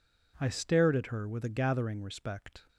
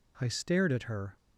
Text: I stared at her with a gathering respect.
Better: first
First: none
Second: stops before "with a gathering respect"; at 1.1 s

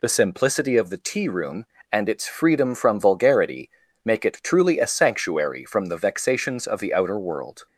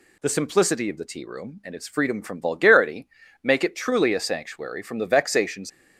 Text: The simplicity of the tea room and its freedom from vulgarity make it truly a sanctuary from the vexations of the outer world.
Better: first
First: pauses between "vulgarity" and "make"; slight; at 3.7 s; 0.34 s long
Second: pauses between "vulgarity" and "make"; at 3.0 s; 0.38 s long // stops before "of the outer world"; at 5.6 s

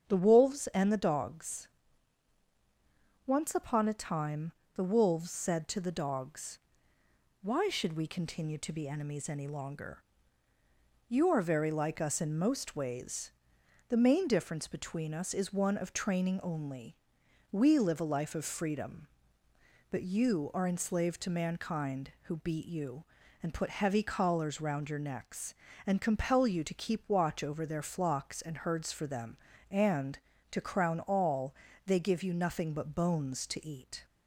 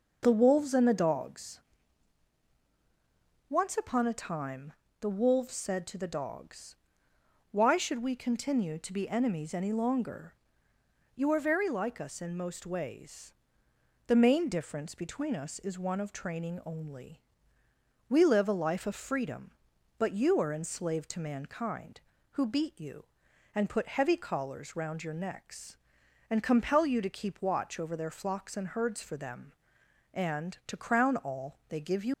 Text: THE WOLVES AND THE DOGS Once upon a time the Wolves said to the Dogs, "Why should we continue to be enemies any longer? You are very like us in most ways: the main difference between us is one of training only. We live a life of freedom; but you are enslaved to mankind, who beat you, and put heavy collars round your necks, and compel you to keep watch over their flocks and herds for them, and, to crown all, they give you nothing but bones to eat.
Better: first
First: starts louder than the rest; strong; until 1.0 s; 7.5 dB // pauses between "DOGS" and "Once"; strong; at 1.6 s; 1.5 s long // pauses between "time" and "the"; slight; at 4.5 s; 0.22 s long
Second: starts louder than the rest; noticeable; until 1.2 s; 6 dB // pauses between "DOGS" and "Once"; strong; at 1.5 s; 1.9 s long // pauses between "time" and "the"; slight; at 4.7 s; 0.30 s long // stops before "nothing but bones to eat"; at 32.1 s

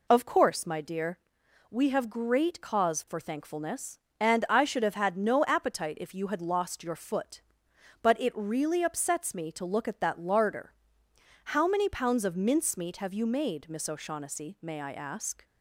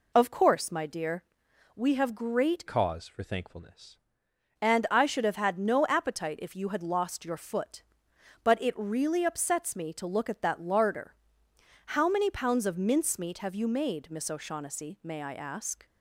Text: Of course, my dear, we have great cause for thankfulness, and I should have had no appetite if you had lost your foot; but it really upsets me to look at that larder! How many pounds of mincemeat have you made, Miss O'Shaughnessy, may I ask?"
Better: first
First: none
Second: changes voice from "cause" to "thankfulness"; from 2.6 to 3.9 s; 1.3 s long

